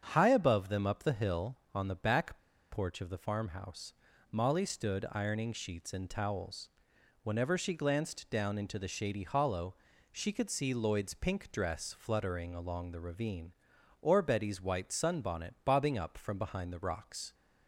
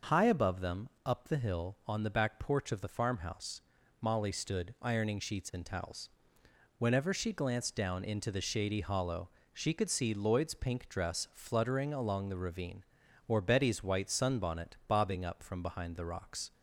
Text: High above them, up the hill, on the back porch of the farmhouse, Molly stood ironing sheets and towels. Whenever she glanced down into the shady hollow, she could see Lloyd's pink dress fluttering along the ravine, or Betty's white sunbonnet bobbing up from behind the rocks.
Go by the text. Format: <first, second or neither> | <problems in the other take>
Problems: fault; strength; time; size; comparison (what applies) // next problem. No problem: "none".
second | starts louder than the rest; strong; until 1.0 s; 7.5 dB // pauses between "back" and "porch"; slight; at 2.3 s; 0.34 s long